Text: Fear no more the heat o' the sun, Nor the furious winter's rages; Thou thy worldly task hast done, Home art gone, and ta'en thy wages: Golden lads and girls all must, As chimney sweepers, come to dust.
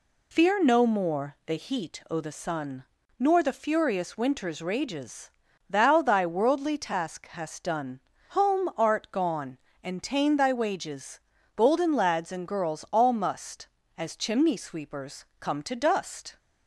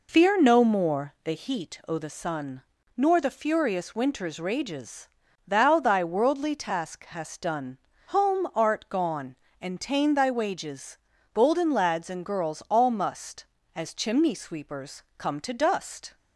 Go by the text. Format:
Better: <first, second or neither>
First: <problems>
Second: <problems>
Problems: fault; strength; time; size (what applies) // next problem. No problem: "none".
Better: first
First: none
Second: starts louder than the rest; noticeable; until 1.1 s; 4 dB